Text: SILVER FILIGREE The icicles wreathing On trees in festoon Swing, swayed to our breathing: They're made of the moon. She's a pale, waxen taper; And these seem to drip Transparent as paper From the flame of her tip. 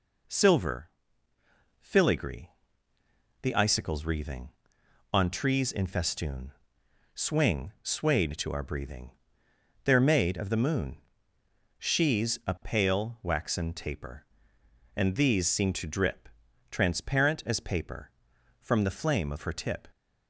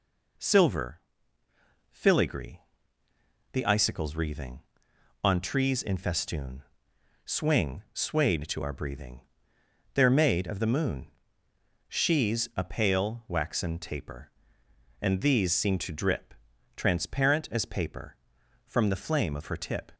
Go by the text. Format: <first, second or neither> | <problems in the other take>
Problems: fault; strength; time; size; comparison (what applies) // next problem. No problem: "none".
neither | pauses between "SILVER" and "FILIGREE"; noticeable; the same in both // pauses between "FILIGREE" and "The"; noticeable; the same in both // pauses between "festoon" and "Swing"; noticeable; the same in both // pauses between "drip" and "Transparent"; the same in both